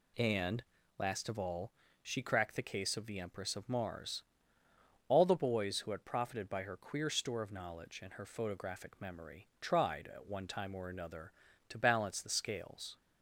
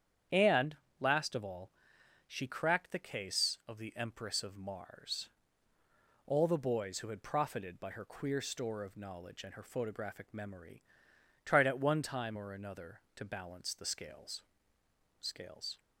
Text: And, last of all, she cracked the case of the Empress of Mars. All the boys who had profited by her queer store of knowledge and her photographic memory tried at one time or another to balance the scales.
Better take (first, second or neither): first